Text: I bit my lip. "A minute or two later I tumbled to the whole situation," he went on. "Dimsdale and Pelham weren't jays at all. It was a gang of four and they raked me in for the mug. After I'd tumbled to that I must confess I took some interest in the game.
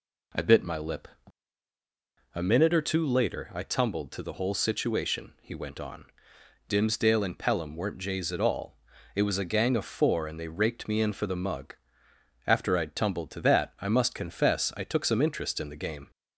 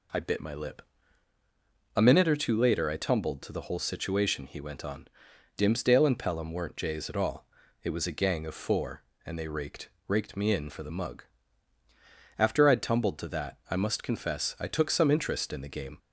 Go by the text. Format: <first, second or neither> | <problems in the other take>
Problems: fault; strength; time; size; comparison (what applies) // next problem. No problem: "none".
first | says "raked" twice; at 10.0 s